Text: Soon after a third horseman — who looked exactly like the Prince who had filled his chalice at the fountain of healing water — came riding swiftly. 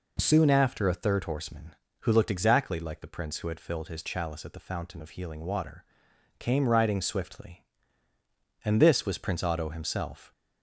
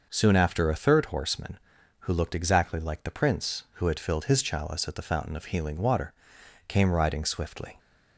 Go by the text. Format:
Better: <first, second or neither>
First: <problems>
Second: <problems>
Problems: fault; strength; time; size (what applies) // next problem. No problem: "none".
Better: second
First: goes on to say "And this was Prince Otto himself"; strong; from 8.6 s on; 1.6 s long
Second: none